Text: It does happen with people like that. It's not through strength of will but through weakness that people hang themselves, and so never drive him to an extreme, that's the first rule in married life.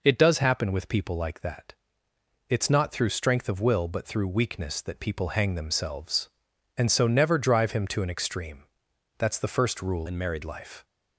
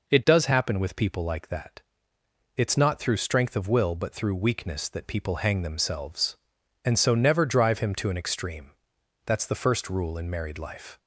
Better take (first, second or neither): second